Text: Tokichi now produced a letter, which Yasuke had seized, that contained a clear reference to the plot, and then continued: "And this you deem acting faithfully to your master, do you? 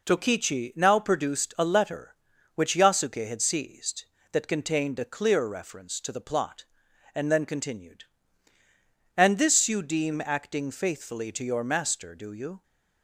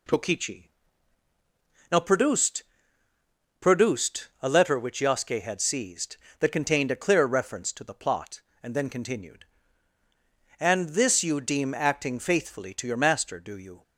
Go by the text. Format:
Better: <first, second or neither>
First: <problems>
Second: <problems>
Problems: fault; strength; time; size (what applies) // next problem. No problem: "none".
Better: first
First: none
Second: pauses between "Tokichi" and "now"; at 0.6 s; 1.2 s long // says "produced" twice; at 3.5 s